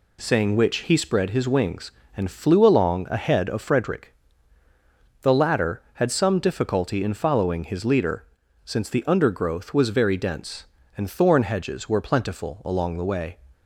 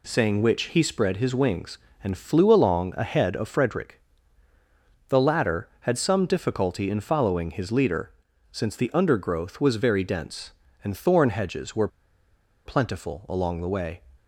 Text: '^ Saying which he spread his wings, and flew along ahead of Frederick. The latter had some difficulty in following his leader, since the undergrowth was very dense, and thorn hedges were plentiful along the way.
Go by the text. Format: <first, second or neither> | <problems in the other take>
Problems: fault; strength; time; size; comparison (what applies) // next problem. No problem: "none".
first | pauses between "were" and "plentiful"; noticeable; at 11.8 s; 0.78 s long